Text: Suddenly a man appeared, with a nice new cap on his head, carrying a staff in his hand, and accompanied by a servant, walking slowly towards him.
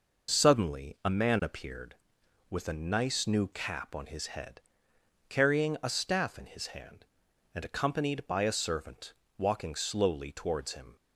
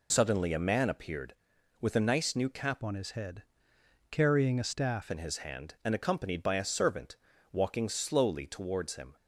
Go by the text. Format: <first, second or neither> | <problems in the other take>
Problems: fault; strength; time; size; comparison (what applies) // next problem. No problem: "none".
first | changes voice from "on" to "staff"; from 2.8 to 5.0 s; 2.2 s long